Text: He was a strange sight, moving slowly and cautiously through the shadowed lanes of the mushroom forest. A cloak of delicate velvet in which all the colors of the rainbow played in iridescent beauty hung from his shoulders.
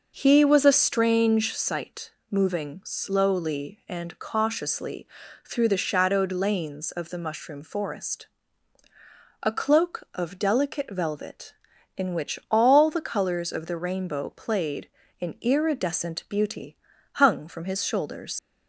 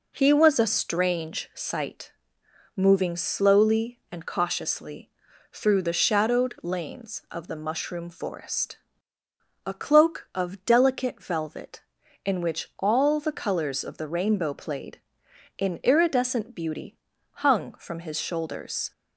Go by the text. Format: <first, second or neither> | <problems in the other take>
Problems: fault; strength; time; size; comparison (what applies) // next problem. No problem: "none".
second | pauses between "cautiously" and "through"; slight; at 5.0 s; 0.36 s long; also in the second // pauses between "beauty" and "hung"; slight; at 16.7 s; 0.36 s long; also in the second // leaves "shoulders" unfinished; at 18.3 s; 60 ms